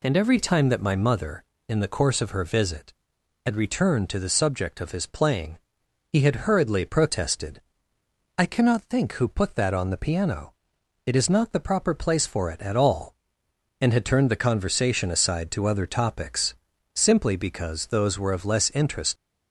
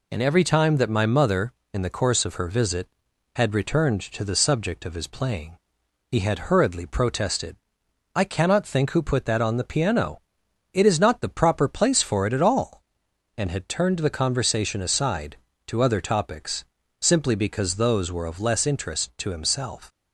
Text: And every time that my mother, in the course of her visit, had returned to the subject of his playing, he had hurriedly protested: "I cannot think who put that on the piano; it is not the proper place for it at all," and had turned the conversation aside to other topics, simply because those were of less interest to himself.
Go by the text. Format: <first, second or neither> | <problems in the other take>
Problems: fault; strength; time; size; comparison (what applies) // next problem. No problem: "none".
second | stops before "to himself"; at 19.1 s